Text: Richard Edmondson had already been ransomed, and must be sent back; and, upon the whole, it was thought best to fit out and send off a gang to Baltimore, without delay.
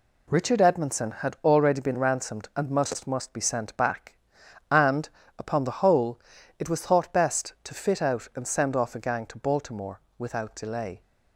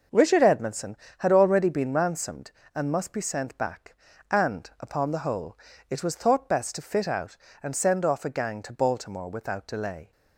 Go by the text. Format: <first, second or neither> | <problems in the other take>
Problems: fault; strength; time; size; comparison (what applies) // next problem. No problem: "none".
second | says "must" twice; at 3.0 s